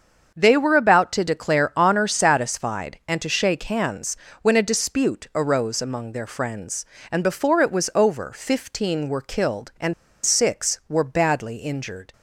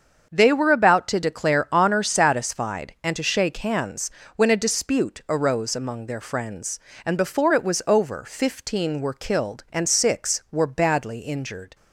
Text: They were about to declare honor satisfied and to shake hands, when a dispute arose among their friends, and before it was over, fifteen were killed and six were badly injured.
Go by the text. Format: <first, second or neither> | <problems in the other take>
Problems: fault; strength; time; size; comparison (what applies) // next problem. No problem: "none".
second | starts louder than the rest; until 1.3 s; 7 dB; also in the second // pauses between "and" and "six"; slight; at 9.9 s; 0.30 s long